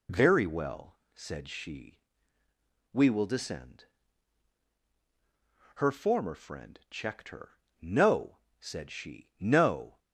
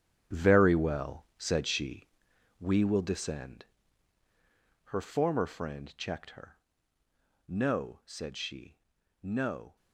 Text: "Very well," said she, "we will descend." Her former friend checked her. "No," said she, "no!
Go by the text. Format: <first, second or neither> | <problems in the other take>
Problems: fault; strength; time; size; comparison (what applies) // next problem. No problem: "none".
first | gets quieter; strong; throughout; 11 dB